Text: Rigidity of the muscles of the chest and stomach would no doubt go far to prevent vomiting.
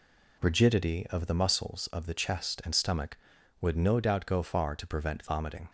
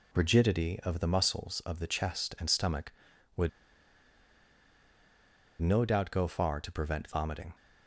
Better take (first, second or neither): first